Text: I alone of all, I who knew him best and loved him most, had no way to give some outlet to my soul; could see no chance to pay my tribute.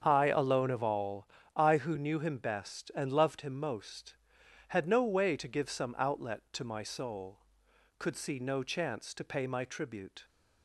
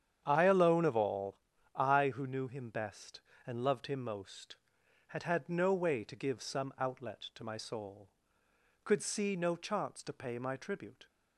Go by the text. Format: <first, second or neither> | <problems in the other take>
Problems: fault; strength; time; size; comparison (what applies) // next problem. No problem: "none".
first | starts louder than the rest; strong; until 1.2 s; 8.5 dB; strong in the first // says "had" twice; at 5.2 s